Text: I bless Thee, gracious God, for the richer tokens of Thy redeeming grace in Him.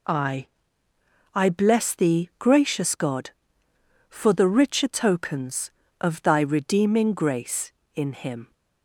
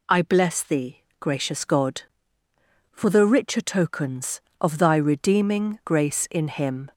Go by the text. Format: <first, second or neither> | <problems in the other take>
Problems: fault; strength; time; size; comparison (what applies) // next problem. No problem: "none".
second | says "I" twice; at 1.3 s